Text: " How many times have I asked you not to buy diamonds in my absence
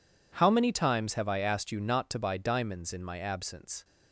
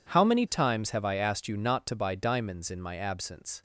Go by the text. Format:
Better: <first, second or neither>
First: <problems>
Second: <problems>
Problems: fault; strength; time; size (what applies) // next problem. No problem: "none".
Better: neither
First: none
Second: none